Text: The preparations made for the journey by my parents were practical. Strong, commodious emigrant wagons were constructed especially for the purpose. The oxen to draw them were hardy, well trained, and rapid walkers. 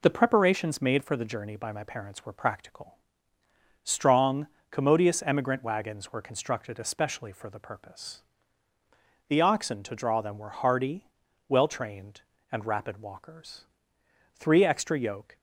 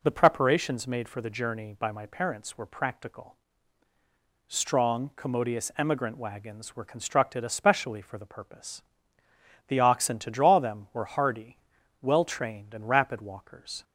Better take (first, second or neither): second